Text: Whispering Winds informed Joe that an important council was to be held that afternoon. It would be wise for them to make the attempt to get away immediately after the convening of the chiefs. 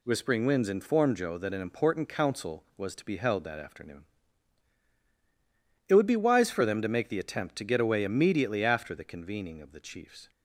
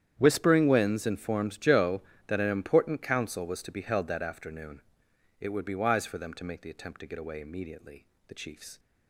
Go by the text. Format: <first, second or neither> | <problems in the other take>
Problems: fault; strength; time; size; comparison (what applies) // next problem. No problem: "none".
first | starts louder than the rest; strong; until 1.1 s; 9.5 dB // skips "after the convening of"; at 8.1 s